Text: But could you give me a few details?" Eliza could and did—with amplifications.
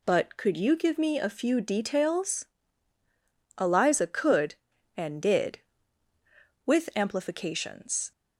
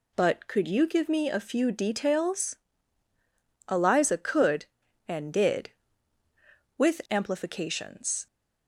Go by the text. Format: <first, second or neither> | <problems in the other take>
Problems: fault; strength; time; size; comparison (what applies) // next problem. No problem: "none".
neither | none